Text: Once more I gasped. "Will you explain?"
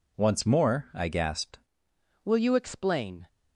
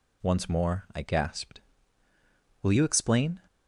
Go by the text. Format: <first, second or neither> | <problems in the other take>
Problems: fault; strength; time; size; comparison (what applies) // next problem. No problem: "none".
second | changes voice at "Will"; from 2.2 s on; 1.0 s long